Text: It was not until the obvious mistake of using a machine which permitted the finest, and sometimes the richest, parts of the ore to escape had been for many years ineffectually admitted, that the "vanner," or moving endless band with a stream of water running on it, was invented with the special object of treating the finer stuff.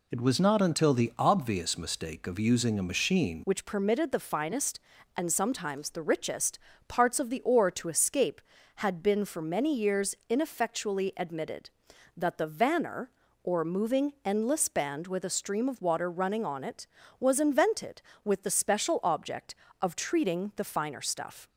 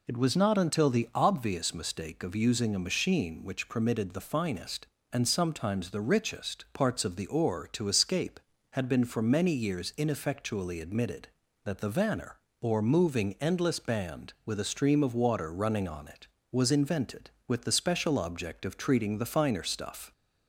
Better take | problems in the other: second | changes voice at "which"; from 3.4 s on; 18.0 s long

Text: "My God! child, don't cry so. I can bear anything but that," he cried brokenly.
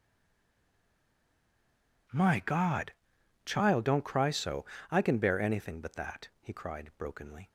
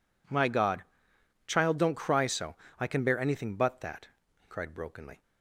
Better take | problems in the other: second | stays silent before the first word; noticeable; until 2.0 s; 2.0 s long

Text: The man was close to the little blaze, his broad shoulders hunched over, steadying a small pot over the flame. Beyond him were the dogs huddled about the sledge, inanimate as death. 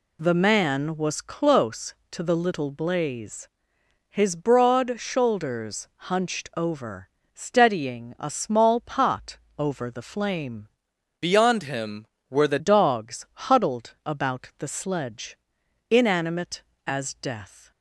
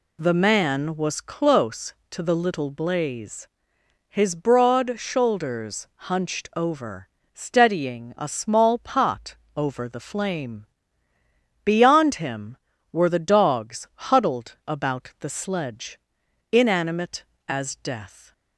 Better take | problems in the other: second | pauses between "shoulders" and "hunched"; slight; at 5.8 s; 0.22 s long; slight in the second // pauses between "pot" and "over"; slight; at 9.3 s; 0.18 s long; slight in the second // changes voice from "Beyond" to "the"; from 11.2 to 12.5 s; 1.3 s long // pauses between "dogs" and "huddled"; slight; at 13.2 s; 0.22 s long; slight in the second

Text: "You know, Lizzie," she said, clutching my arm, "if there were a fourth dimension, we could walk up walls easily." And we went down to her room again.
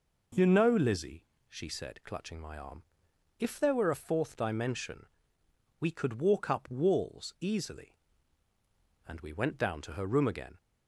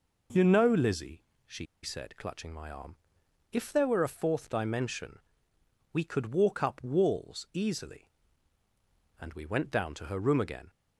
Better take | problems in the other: first | pauses between "she" and "said"; slight; at 1.6 s; 0.17 s long

